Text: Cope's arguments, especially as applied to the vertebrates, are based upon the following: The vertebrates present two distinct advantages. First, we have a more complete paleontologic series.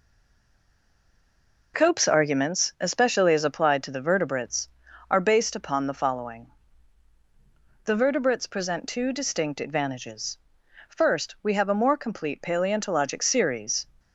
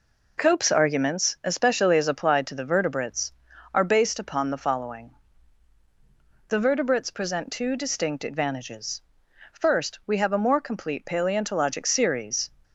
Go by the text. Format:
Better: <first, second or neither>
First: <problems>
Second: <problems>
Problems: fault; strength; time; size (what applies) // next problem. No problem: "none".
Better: second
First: stays silent before the first word; noticeable; until 1.7 s; 1.7 s long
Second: none